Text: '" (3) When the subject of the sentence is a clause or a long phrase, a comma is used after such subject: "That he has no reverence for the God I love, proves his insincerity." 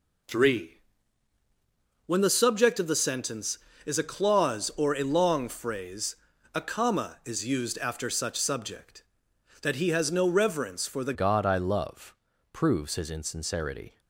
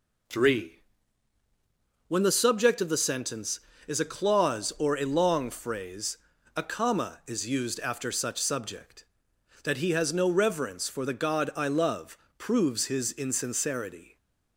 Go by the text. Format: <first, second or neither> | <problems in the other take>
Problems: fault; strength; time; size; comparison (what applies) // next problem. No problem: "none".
second | changes voice at "God"; from 11.1 s on; 2.8 s long